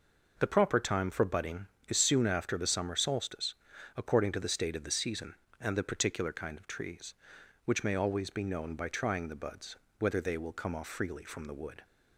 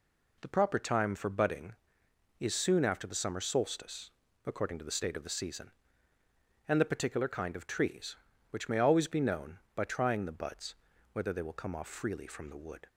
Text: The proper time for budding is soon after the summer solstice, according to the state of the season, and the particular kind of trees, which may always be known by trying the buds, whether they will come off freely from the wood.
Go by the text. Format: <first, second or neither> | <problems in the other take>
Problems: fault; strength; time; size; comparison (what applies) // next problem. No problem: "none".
neither | none